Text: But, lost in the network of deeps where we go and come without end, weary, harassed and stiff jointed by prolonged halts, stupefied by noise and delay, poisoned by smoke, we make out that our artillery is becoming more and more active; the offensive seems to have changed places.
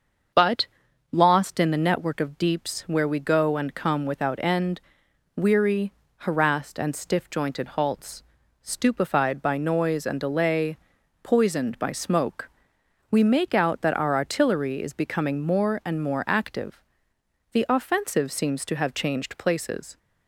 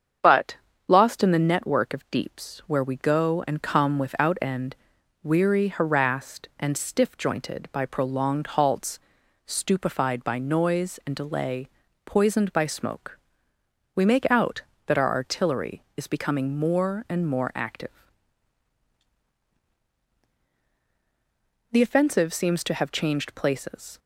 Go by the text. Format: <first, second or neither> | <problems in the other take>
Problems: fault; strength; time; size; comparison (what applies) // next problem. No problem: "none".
second | starts louder than the rest; until 1.8 s; 6.5 dB; strong in the second // skips "by prolonged"; at 7.6 s